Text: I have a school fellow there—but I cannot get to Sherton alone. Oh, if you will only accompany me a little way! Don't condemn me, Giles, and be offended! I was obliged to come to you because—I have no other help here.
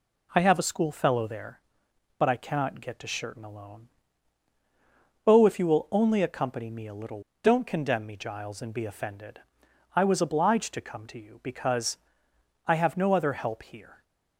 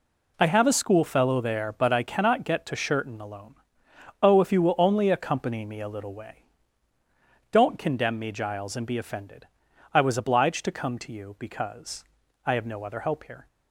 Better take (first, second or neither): second